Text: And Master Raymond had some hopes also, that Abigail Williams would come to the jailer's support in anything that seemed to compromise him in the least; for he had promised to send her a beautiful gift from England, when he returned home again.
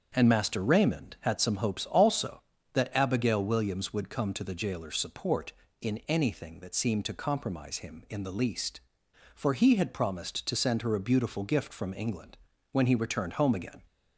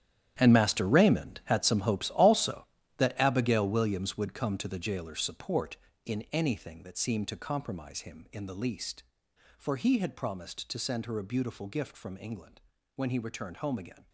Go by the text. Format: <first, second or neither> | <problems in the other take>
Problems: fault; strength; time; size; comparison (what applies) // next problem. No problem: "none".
first | gets quieter; strong; throughout; 13.5 dB // starts louder than the rest; strong; until 1.4 s; 10.5 dB; also in the first